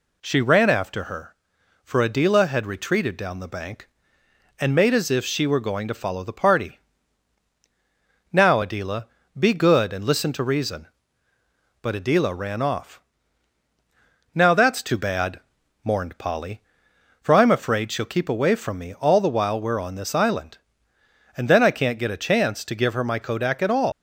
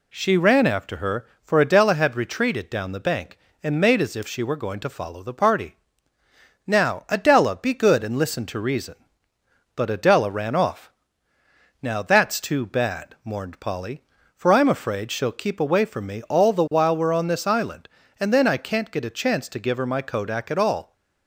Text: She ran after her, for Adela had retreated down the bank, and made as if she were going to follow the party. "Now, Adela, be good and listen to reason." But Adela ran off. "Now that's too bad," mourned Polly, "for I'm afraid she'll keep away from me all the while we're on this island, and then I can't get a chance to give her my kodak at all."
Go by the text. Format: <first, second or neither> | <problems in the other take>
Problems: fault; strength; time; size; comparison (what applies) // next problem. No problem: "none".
second | leaves "all" unfinished; at 23.9 s; 140 ms